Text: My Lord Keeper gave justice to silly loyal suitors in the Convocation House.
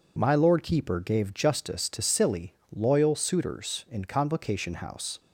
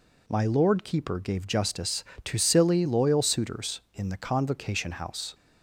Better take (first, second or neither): second